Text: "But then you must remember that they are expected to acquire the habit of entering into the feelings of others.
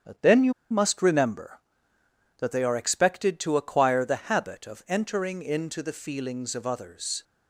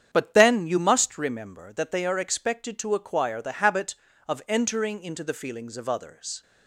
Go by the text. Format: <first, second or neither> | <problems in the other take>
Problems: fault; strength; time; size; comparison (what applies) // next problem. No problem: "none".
second | starts louder than the rest; strong; until 1.2 s; 8.5 dB; strong in the second // pauses between "you" and "must"; slight; at 0.5 s; 0.18 s long